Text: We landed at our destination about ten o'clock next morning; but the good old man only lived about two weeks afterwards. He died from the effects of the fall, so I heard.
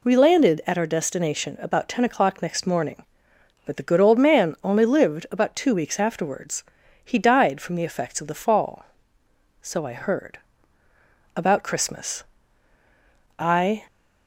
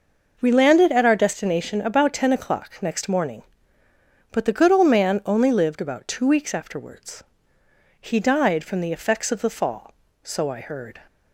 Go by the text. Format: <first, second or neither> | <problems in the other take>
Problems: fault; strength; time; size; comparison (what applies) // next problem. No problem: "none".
second | goes on to say "About Christmas I"; strong; from 11.3 s on; 2.4 s long